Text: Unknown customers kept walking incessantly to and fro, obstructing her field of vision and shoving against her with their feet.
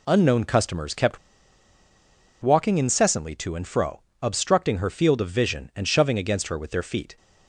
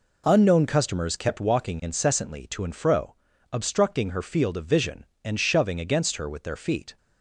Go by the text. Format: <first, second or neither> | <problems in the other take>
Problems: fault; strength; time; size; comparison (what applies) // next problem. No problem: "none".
second | pauses between "kept" and "walking"; at 1.1 s; 1.2 s long